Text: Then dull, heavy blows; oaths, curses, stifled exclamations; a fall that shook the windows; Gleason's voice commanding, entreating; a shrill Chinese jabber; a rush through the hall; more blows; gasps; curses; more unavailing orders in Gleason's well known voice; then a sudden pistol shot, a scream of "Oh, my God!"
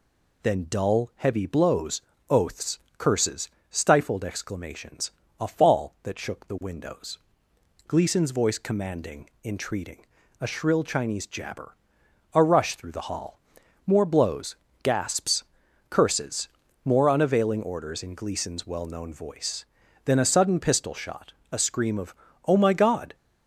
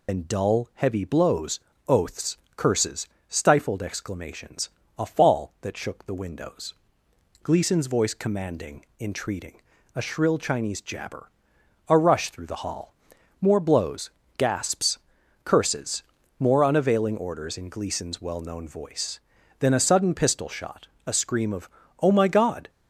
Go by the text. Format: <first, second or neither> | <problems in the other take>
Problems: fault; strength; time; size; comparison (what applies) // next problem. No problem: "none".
first | loses the start of "Then"; at 0.0 s; 85 ms // pauses between "of" and "Oh"; slight; at 21.6 s; 0.32 s long; slight in the first